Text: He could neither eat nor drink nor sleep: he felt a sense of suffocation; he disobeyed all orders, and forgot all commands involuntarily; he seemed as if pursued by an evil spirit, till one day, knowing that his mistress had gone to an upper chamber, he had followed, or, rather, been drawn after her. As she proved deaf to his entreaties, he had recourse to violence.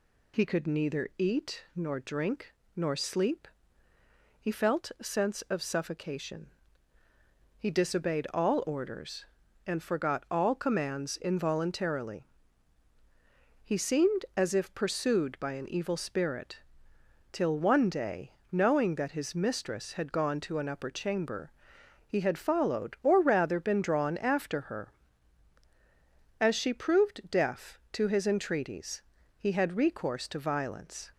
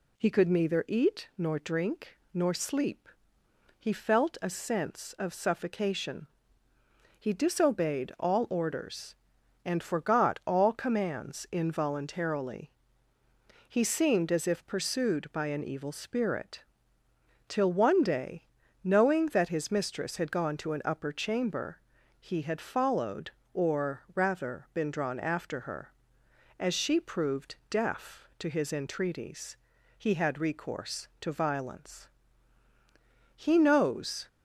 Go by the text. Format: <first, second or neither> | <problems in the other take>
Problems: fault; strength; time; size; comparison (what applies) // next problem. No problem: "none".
first | pauses between "drink" and "nor"; slight; at 2.1 s; 0.16 s long; slight in the first // goes on to say "He knows"; noticeable; from 33.3 s on; 0.92 s long